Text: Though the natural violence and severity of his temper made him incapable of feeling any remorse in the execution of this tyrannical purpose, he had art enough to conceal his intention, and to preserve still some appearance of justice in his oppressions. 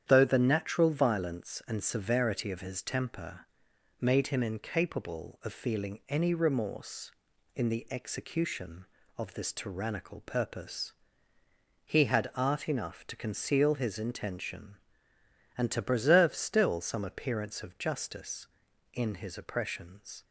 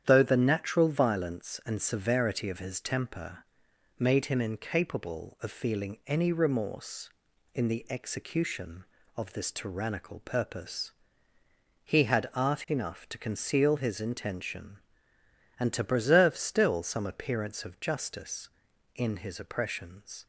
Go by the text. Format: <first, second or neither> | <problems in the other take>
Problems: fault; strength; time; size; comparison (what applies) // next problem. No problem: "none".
neither | starts louder than the rest; strong; the same in both // pauses between "temper" and "made"; noticeable; the same in both